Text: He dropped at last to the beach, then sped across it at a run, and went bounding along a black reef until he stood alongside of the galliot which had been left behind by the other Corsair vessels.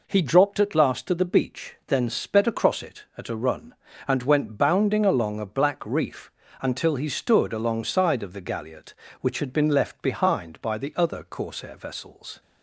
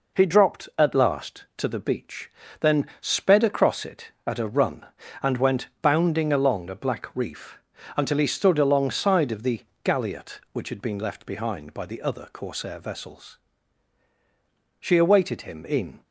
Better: first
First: pauses between "reef" and "until"; slight; at 6.3 s; 0.30 s long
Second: pauses between "reef" and "until"; at 7.5 s; 0.38 s long // pauses between "the" and "galliot"; slight; at 9.6 s; 0.20 s long // goes on to say "She awaited him in"; noticeable; from 14.7 s on; 1.2 s long

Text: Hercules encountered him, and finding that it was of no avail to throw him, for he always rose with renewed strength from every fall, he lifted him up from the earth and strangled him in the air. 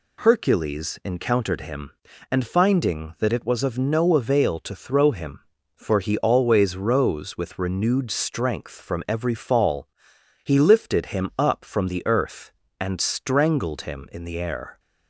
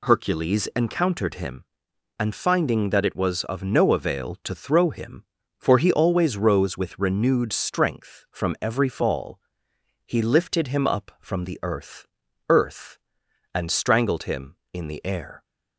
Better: first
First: none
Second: says "earth" twice; at 12.4 s

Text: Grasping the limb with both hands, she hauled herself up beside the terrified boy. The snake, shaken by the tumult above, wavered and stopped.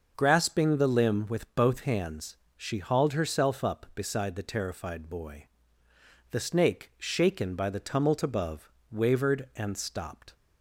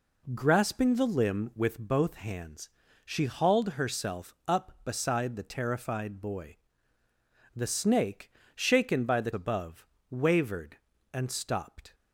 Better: first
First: none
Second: skips "tumult"; at 9.3 s

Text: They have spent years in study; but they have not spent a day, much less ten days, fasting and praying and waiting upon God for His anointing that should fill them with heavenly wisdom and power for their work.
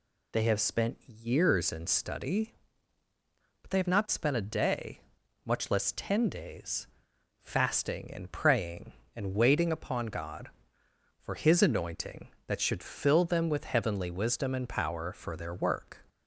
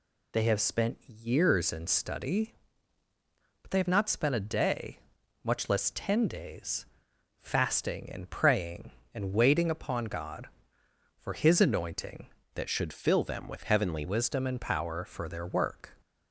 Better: first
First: none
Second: changes voice from "that" to "heavenly"; from 12.5 to 14.0 s; 1.5 s long

